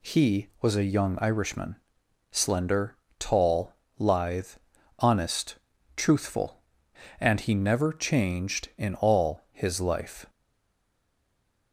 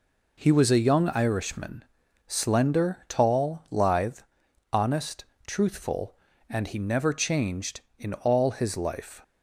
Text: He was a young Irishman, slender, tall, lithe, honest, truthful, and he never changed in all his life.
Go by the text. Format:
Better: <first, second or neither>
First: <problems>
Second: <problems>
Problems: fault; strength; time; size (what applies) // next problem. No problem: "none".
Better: second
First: stays silent after the last word; noticeable; from 10.2 s on; 1.5 s long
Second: none